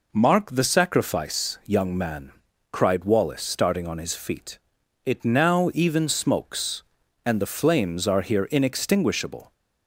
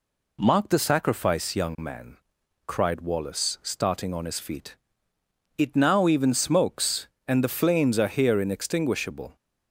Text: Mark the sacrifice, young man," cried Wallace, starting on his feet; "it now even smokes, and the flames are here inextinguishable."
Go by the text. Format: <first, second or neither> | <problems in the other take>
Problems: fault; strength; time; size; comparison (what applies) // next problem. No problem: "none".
neither | none